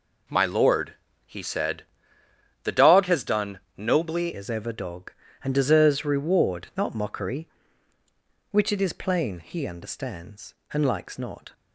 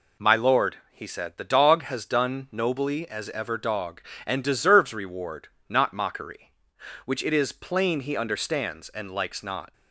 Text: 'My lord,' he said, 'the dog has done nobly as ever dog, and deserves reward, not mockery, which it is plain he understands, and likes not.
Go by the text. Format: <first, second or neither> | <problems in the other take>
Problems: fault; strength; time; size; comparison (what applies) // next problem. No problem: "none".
second | pauses between "done" and "nobly"; slight; at 3.6 s; 0.16 s long // changes voice at "as"; from 4.3 s on; 7.2 s long